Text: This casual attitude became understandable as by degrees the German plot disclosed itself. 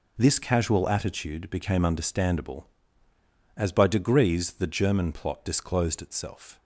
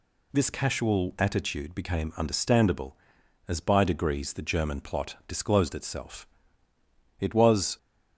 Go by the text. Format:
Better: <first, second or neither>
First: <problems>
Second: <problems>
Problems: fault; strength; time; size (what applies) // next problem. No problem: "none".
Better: first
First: none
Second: goes on to say "It was"; from 7.1 s on; 0.58 s long